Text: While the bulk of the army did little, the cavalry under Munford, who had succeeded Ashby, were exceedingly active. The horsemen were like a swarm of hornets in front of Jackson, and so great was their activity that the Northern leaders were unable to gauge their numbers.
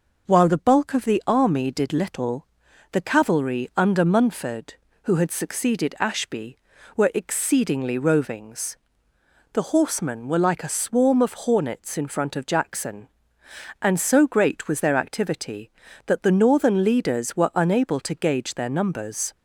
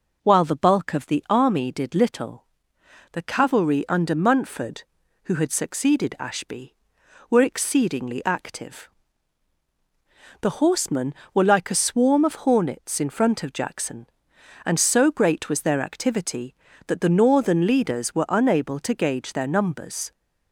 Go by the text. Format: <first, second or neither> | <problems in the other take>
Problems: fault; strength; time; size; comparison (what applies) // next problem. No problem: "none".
second | says "rovings" for "active"; at 7.9 s